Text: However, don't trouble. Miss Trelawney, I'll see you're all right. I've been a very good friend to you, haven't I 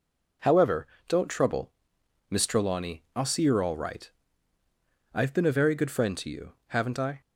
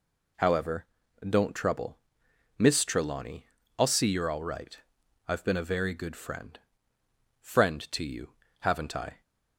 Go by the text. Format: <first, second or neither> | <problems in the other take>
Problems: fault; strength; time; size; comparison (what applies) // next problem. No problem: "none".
first | says "friend" twice; at 7.4 s